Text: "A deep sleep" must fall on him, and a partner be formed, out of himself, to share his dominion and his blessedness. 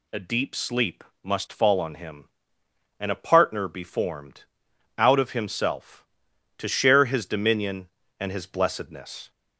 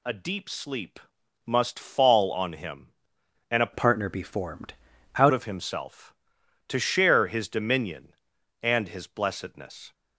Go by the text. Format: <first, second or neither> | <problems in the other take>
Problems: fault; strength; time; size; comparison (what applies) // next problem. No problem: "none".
first | pauses between "sleep" and "must"; at 1.0 s; 0.44 s long; slight in the first // changes voice from "partner" to "out"; from 3.7 to 5.3 s; 1.6 s long